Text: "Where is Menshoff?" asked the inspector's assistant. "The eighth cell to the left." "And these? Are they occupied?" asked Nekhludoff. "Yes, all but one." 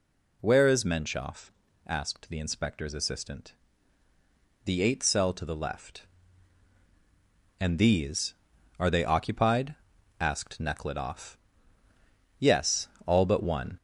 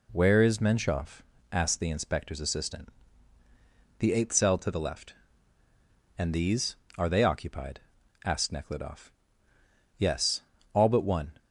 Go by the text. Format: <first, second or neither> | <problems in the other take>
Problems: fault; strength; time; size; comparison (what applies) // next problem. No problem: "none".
second | gets louder; throughout; 3.5 dB